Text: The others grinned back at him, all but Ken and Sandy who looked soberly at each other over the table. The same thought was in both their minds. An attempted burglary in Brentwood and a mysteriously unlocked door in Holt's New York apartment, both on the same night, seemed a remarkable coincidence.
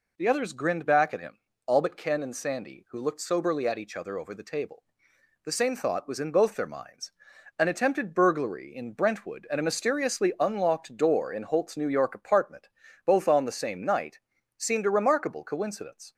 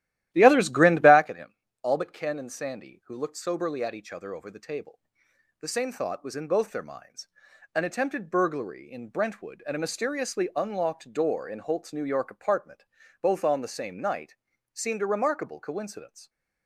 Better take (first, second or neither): first